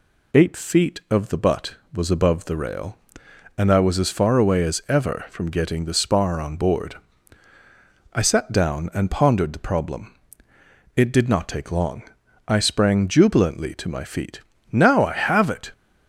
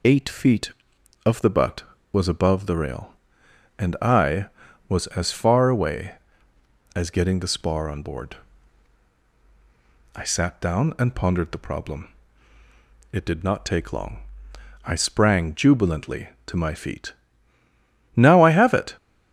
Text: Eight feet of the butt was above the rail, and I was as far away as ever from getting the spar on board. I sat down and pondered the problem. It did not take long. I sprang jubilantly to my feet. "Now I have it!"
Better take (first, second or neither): first